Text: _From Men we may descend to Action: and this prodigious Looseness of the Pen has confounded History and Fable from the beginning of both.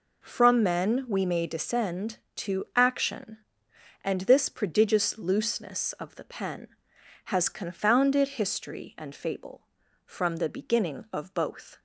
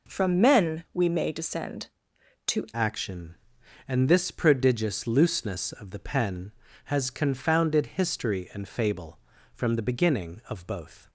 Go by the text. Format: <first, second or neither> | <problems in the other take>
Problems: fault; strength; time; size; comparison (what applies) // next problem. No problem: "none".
first | changes voice at "Action"; from 2.7 s on; 8.3 s long